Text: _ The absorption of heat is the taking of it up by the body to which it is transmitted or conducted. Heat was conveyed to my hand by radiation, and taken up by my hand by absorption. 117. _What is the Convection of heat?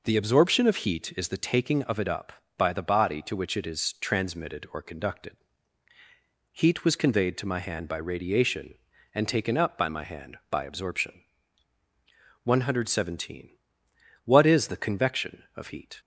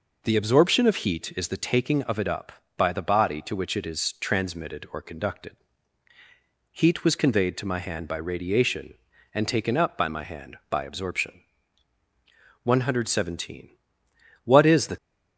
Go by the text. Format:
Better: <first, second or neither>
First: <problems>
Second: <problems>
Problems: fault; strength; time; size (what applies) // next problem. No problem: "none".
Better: first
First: none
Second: stops before "Convection of heat"; at 14.9 s